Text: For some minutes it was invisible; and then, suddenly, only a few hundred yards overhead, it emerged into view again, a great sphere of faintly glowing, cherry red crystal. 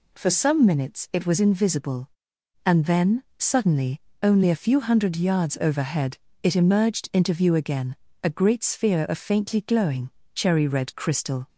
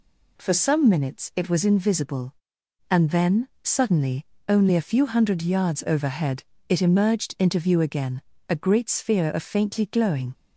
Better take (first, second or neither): first